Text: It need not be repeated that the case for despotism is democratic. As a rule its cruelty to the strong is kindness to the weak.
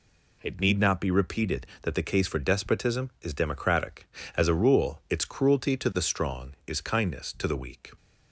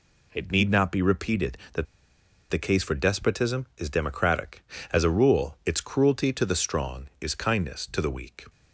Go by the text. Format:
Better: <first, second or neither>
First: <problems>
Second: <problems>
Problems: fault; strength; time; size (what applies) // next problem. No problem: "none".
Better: first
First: none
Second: pauses between "that" and "the"; noticeable; at 1.8 s; 0.65 s long